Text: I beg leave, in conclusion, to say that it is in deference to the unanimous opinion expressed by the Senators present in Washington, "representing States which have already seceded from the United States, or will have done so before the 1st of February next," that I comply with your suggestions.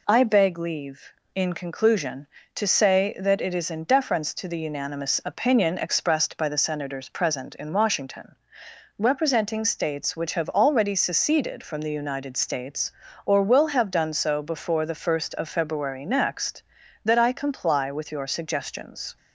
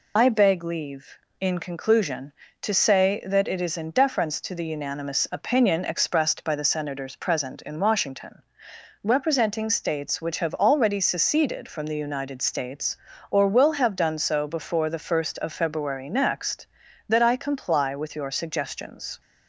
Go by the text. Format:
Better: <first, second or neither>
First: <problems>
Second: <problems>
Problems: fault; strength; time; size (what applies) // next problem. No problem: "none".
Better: first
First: none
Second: loses the start of "I"; at 0.1 s; 35 ms